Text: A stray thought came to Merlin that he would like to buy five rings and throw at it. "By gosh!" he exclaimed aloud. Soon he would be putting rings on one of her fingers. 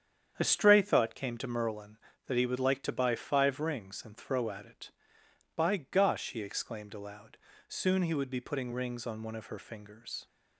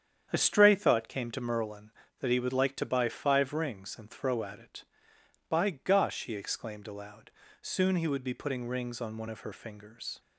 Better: neither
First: starts louder than the rest; strong; until 1.3 s; 8.5 dB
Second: starts louder than the rest; strong; until 1.3 s; 8.5 dB

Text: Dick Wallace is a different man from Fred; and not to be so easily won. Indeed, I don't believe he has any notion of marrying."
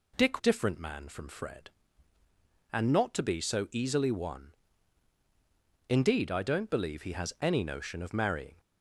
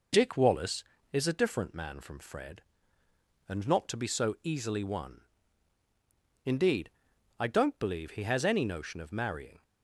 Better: second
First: skips "Wallace is a"; at 0.3 s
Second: none

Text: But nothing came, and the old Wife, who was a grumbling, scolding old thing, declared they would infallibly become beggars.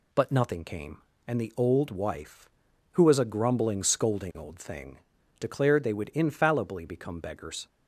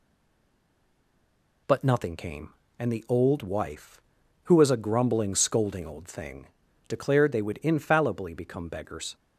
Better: first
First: none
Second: stays silent before the first word; noticeable; until 1.6 s; 1.6 s long

